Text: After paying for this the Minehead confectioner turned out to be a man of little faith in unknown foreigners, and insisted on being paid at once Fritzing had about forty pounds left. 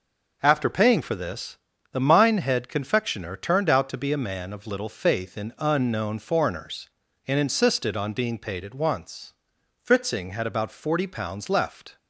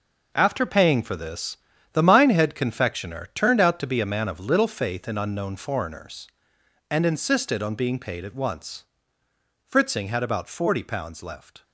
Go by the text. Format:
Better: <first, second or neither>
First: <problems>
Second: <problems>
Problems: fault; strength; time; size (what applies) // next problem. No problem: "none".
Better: first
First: pauses between "this" and "the"; slight; at 1.5 s; 0.34 s long // pauses between "once" and "Fritzing"; noticeable; at 9.3 s; 0.48 s long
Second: gets quieter; strong; throughout; 10.5 dB // pauses between "this" and "the"; slight; at 1.5 s; 0.36 s long // pauses between "once" and "Fritzing"; noticeable; at 8.8 s; 0.80 s long